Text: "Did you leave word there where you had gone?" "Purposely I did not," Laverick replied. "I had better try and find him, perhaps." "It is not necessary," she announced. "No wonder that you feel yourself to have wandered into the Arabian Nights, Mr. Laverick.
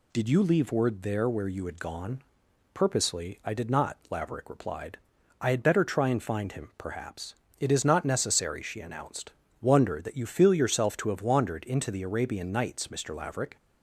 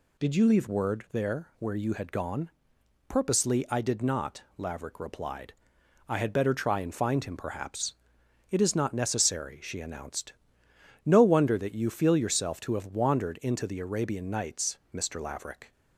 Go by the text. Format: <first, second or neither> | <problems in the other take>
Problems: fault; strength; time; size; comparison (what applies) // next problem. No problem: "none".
second | skips "No"; at 9.4 s